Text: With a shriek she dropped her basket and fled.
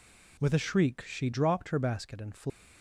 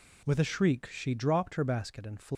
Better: neither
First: none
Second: none

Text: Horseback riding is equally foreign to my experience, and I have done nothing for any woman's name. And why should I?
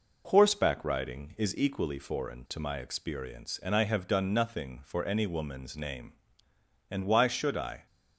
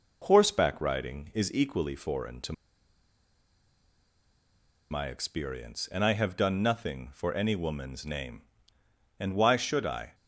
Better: first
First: none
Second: pauses between "to" and "my"; strong; at 2.5 s; 2.3 s long

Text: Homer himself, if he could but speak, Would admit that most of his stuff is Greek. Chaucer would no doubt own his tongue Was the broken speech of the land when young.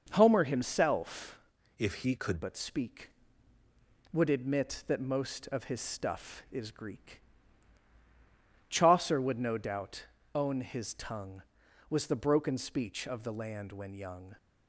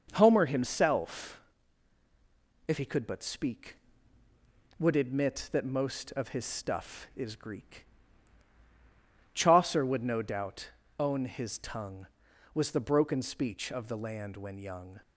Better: second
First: changes voice from "if" to "could"; from 1.7 to 2.4 s; 0.7 s long // pauses between "doubt" and "own"; slight; at 10.0 s; 0.30 s long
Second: pauses between "doubt" and "own"; slight; at 10.6 s; 0.30 s long

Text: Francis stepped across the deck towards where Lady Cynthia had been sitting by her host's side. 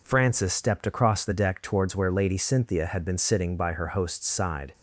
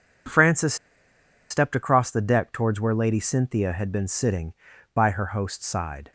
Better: first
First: none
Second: pauses between "Francis" and "stepped"; noticeable; at 0.7 s; 0.75 s long

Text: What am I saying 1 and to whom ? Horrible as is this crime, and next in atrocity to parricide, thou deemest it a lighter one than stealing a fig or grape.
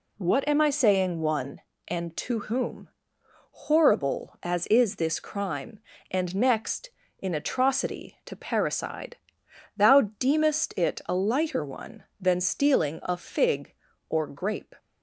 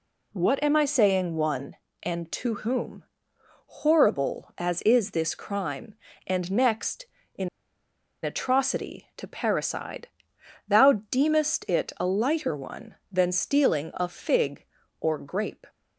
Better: first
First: none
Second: pauses between "in" and "atrocity"; noticeable; at 7.4 s; 0.75 s long

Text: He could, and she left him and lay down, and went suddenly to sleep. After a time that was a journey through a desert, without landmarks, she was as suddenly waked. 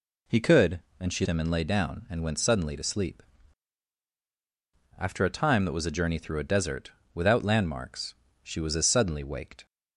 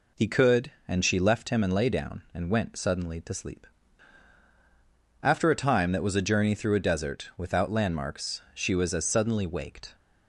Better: second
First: skips "left"; at 1.2 s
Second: none

